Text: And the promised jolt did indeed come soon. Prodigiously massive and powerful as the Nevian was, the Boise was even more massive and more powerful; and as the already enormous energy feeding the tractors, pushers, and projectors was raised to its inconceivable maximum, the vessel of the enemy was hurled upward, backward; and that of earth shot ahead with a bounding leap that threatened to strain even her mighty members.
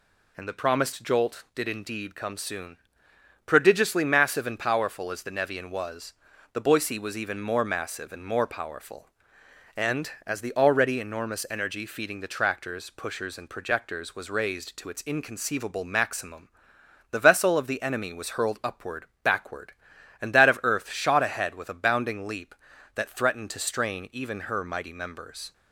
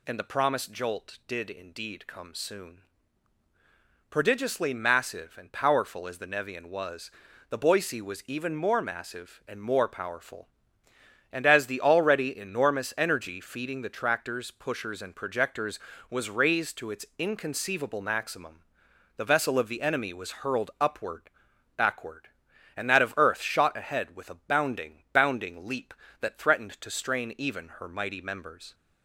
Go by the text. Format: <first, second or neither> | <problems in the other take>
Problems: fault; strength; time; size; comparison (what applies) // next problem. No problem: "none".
first | says "bounding" twice; at 25.1 s